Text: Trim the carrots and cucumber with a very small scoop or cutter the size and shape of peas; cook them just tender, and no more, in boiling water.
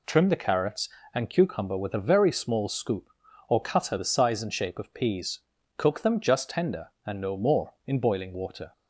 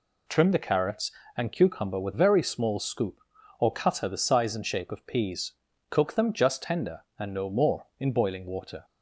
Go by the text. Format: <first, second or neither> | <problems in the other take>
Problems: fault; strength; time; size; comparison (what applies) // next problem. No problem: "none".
first | skips "a"; at 2.1 s